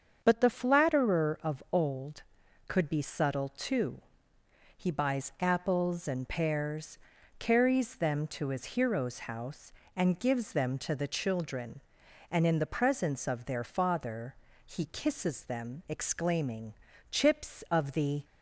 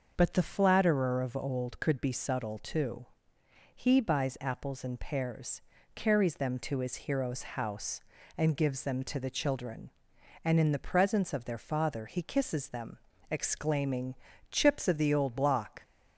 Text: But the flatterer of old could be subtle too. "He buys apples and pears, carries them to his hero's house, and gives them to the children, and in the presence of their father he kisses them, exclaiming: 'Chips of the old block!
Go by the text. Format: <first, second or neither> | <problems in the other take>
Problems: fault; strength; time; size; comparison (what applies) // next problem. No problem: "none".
second | starts louder than the rest; until 1.2 s; 7 dB; noticeable in the second // pauses between "father" and "he"; slight; at 14.3 s; 0.32 s long // stops before "old block"; at 18.2 s